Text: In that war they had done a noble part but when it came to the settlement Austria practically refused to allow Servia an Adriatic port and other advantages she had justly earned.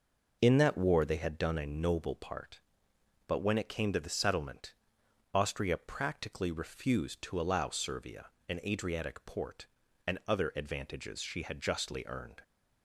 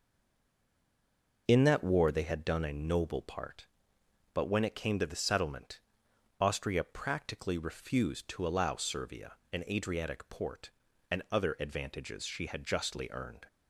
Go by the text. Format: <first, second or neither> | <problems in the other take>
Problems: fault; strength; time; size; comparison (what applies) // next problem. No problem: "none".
first | stays silent before the first word; noticeable; until 1.4 s; 1.4 s long // pauses between "settlement" and "Austria"; noticeable; at 5.7 s; 0.60 s long; noticeable in the first // pauses between "Servia" and "an"; slight; at 9.3 s; 0.15 s long; slight in the first